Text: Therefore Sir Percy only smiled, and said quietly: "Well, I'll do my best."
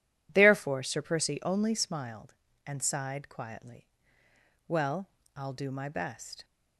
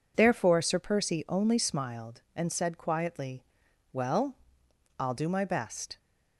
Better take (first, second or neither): second